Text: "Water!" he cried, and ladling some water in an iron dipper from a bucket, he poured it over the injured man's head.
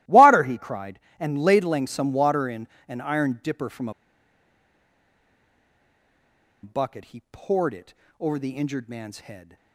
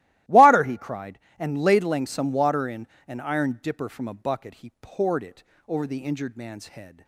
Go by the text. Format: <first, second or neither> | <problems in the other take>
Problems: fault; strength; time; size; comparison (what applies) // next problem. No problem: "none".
second | starts louder than the rest; strong; until 1.2 s; 16 dB; strong in the second // pauses between "in" and "an"; slight; at 2.6 s; 0.20 s long; slight in the second // pauses between "a" and "bucket"; strong; at 3.9 s; 2.7 s long // pauses between "it" and "over"; slight; at 7.9 s; 0.26 s long; slight in the second